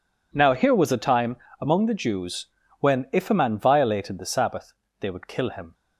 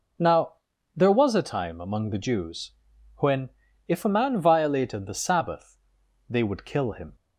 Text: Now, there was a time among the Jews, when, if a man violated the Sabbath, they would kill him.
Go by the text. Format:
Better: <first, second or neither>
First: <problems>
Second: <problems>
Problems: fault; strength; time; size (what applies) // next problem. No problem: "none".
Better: second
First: says "here" for "there"; at 0.5 s // pauses between "time" and "among"; slight; at 1.3 s; 0.24 s long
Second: none